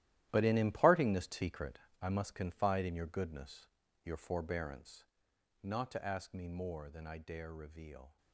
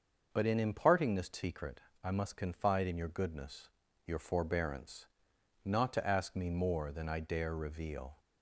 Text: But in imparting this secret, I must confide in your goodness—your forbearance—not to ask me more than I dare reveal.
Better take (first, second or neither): second